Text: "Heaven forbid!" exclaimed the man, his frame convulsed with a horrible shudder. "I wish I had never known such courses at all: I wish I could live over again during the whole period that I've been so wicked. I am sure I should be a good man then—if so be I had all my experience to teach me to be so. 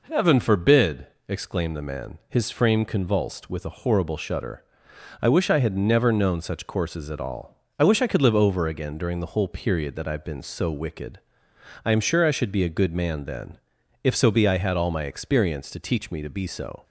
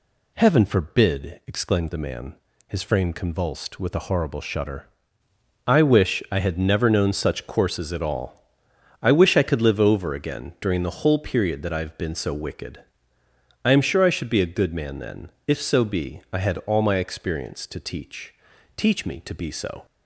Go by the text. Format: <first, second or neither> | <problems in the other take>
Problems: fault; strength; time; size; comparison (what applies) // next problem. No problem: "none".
first | says "teach" twice; at 18.7 s